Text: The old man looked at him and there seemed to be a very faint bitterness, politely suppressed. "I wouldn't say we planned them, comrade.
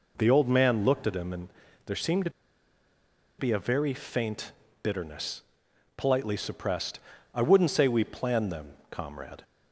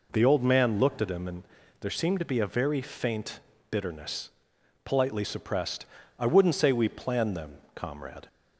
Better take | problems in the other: second | pauses between "and" and "there"; at 1.4 s; 0.38 s long; also in the second // pauses between "to" and "be"; at 2.3 s; 1.0 s long // pauses between "faint" and "bitterness"; slight; at 4.5 s; 0.32 s long; slight in the second

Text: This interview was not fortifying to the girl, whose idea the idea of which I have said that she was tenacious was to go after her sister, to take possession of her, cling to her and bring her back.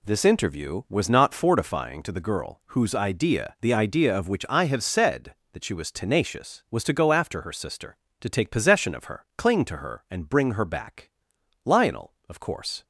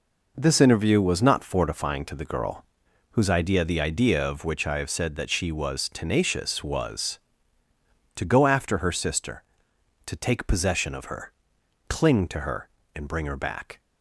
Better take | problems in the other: second | goes on to say "Lionel of course"; noticeable; from 11.6 s on; 1.2 s long

